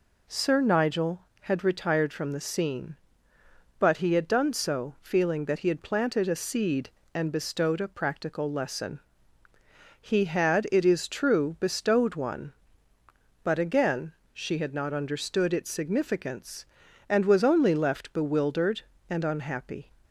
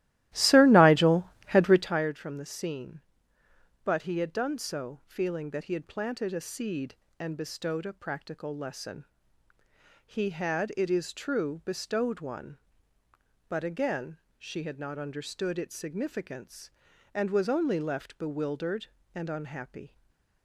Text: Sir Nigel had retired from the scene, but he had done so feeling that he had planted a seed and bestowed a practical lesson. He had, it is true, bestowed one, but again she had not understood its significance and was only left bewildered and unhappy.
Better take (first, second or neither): first